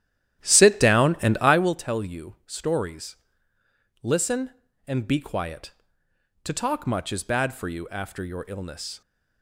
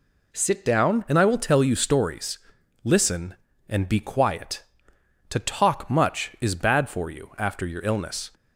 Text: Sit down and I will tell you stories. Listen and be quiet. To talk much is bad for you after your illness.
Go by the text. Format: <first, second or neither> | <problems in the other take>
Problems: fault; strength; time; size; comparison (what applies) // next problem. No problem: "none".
second | starts louder than the rest; strong; until 1.7 s; 12 dB